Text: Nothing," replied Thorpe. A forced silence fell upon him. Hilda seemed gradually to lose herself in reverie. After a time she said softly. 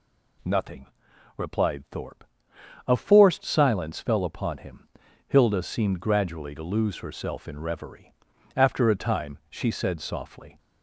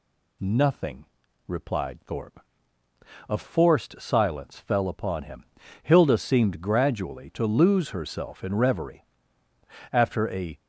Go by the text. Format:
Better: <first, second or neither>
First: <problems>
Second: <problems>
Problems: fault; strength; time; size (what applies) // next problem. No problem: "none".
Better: first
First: none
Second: stops before "time she said softly"; at 10.5 s